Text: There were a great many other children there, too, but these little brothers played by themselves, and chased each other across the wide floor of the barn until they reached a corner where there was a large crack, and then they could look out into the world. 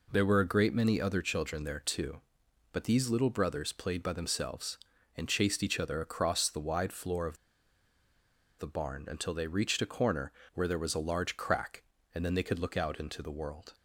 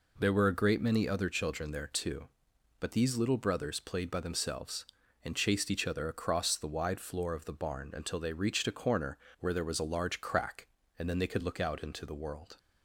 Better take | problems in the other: second | pauses between "of" and "the"; at 7.3 s; 1.2 s long // pauses between "corner" and "where"; slight; at 10.3 s; 0.22 s long; slight in the second

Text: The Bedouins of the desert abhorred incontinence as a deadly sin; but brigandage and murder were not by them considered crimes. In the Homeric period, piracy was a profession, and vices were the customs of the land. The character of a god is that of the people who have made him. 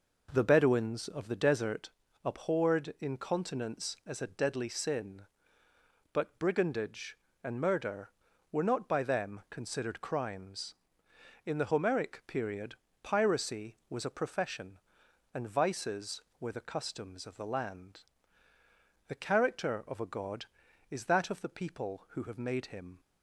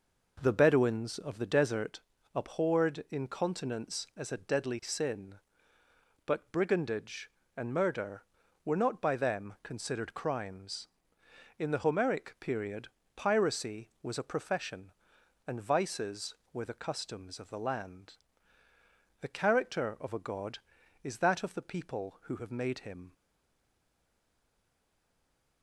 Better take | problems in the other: first | pauses between "desert" and "abhorred"; slight; at 1.9 s; 0.34 s long; slight in the first // stays silent after the last word; from 23.1 s on; 2.5 s long

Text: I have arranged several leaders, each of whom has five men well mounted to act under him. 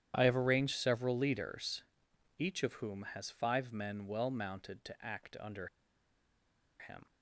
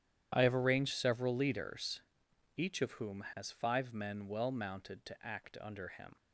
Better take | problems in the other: second | pauses between "under" and "him"; at 5.6 s; 1.1 s long

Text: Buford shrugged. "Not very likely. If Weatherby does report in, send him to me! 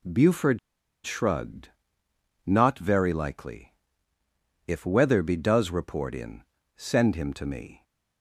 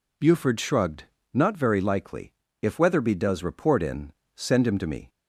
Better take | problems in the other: second | pauses between "Buford" and "shrugged"; noticeable; at 0.5 s; 0.46 s long

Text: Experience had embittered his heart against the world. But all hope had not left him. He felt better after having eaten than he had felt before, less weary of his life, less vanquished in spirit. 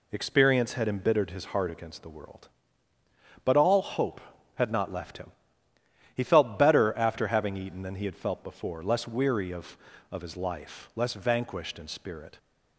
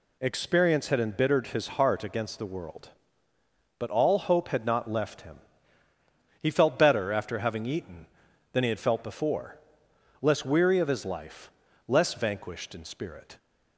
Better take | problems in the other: second | says "of" twice; at 10.0 s

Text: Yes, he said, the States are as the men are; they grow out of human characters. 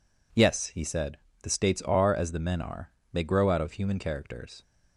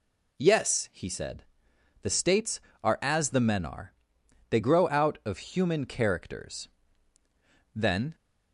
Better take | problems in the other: first | goes on to say "Then"; slight; from 7.7 s on; 0.40 s long

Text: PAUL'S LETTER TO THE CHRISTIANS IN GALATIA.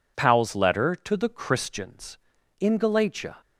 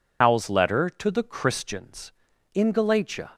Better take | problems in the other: first | loses the start of "PAUL'S"; at 0.2 s; 100 ms

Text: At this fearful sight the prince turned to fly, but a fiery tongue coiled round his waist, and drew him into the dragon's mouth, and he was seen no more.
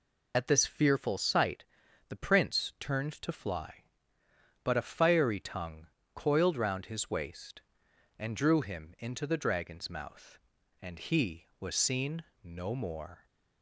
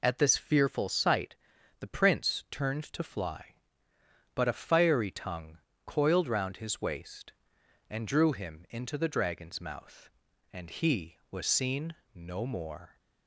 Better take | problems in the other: second | loses the start of "At"; at 0.3 s; 35 ms // pauses between "sight" and "the"; at 1.6 s; 0.42 s long; also in the second // pauses between "tongue" and "coiled"; slight; at 5.8 s; 0.30 s long; slight in the second // pauses between "seen" and "no"; slight; at 12.2 s; 0.18 s long; slight in the second

